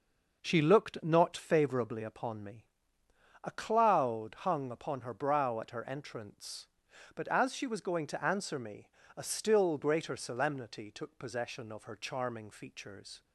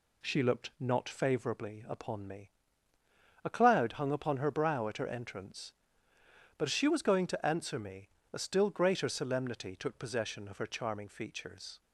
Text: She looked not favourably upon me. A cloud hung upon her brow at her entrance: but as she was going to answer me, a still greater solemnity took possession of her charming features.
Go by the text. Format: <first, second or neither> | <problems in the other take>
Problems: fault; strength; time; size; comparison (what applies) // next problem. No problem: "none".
neither | none